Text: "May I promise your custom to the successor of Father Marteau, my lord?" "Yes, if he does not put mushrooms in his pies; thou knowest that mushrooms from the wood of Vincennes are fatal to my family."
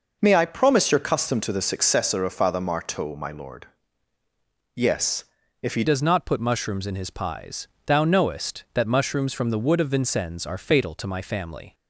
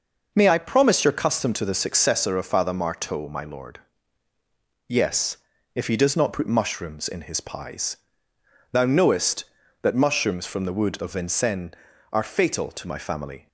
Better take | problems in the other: second | changes voice at "does"; from 5.8 s on; 5.9 s long

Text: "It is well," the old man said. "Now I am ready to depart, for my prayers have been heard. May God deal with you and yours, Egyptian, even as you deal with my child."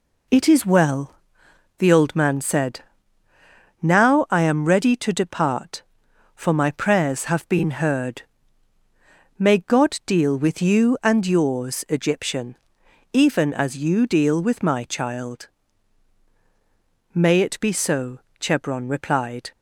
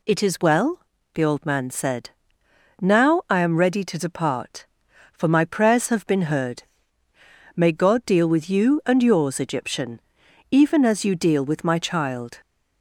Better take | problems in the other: second | goes on to say "May it be so Chebron replied"; strong; from 17.1 s on; 2.3 s long

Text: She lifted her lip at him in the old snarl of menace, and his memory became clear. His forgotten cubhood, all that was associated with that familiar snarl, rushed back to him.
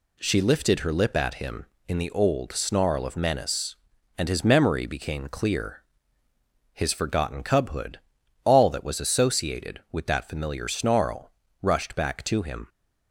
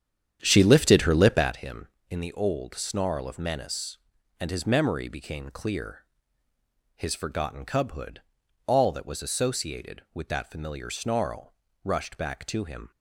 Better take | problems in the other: first | starts louder than the rest; strong; until 1.6 s; 9 dB

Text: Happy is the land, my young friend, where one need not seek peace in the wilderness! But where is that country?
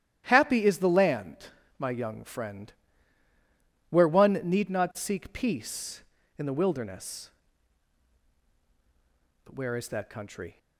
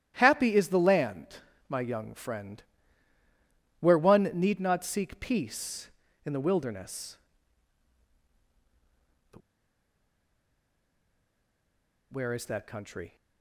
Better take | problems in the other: first | starts louder than the rest; strong; until 1.1 s; 12.5 dB; strong in the first // pauses between "But" and "where"; strong; at 9.4 s; 2.7 s long

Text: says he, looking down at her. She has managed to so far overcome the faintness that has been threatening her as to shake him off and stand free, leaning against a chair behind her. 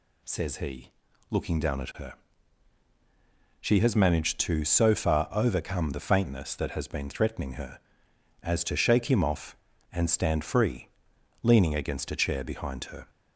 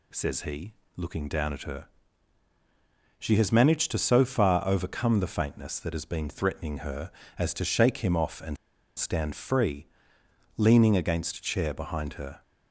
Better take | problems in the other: first | pauses between "and" and "stand"; at 8.5 s; 0.41 s long

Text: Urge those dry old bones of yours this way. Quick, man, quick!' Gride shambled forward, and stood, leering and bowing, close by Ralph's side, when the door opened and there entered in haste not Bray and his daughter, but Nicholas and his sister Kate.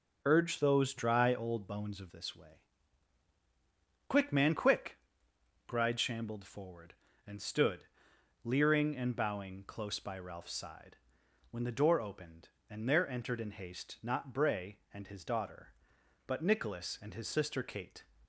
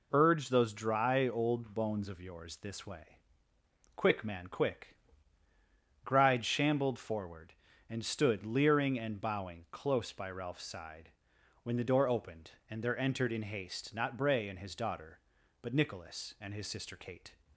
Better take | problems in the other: second | skips "yours"; at 2.0 s

